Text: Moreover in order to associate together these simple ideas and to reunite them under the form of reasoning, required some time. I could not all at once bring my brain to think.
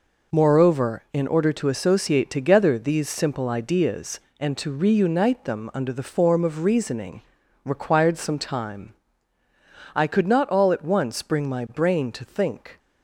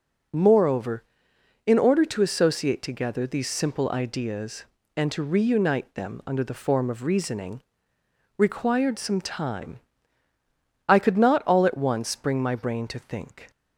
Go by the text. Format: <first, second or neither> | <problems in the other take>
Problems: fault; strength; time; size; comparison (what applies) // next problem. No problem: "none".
neither | none